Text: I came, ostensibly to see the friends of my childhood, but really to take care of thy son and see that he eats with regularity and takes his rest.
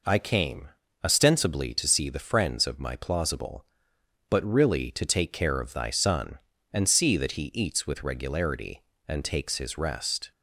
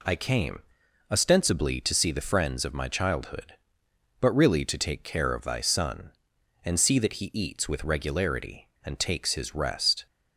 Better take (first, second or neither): second